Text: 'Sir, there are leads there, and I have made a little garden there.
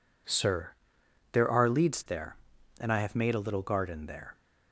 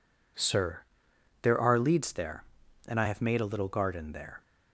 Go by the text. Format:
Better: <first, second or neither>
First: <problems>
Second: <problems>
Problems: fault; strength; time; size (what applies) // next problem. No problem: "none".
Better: neither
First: none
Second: none